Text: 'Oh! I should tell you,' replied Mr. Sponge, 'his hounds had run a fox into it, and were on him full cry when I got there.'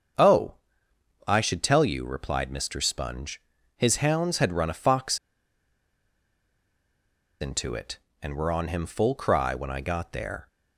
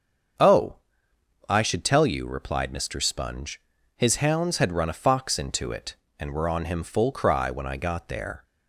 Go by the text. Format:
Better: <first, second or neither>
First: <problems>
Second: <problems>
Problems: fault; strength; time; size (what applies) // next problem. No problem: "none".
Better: second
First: starts louder than the rest; until 1.8 s; 7 dB // pauses between "fox" and "into"; strong; at 5.1 s; 2.2 s long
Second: starts louder than the rest; until 2.1 s; 7 dB